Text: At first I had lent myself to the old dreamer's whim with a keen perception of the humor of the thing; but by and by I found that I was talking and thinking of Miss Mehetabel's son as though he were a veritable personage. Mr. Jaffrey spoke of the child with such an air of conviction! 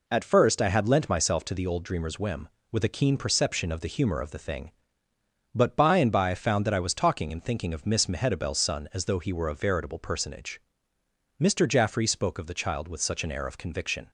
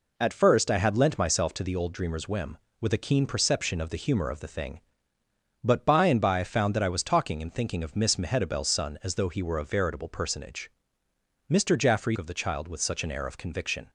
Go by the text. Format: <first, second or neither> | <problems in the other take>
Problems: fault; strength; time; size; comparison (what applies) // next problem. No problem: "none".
first | skips "spoke"; at 12.1 s